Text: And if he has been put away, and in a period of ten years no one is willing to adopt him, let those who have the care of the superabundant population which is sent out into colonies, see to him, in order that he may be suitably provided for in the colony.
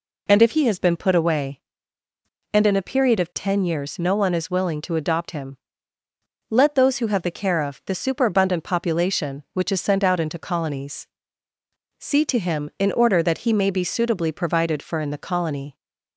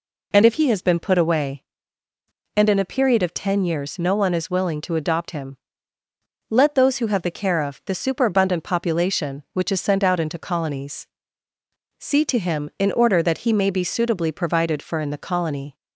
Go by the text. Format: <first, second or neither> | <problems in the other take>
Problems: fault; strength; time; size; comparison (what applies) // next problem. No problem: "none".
neither | none